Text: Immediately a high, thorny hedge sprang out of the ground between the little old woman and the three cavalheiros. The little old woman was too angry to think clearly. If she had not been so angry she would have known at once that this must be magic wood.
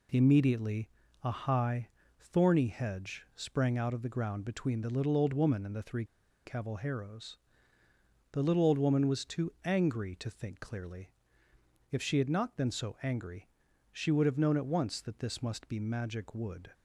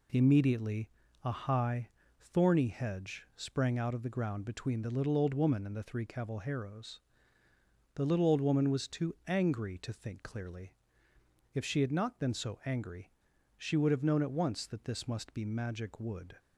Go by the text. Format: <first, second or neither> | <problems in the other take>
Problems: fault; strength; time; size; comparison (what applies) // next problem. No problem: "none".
second | pauses between "Immediately" and "a"; slight; at 0.8 s; 0.34 s long; slight in the second // pauses between "three" and "cavalheiros"; at 6.0 s; 0.40 s long // pauses between "angry" and "she"; at 13.4 s; 0.42 s long; also in the second